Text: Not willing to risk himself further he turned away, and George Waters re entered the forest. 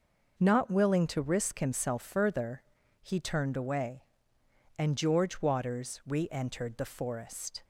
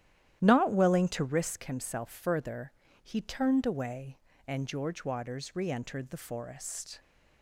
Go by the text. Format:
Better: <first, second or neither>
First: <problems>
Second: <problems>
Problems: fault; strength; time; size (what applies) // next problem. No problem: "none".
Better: first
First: pauses between "further" and "he"; at 2.6 s; 0.40 s long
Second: starts louder than the rest; strong; until 1.5 s; 12 dB // pauses between "further" and "he"; slight; at 2.7 s; 0.32 s long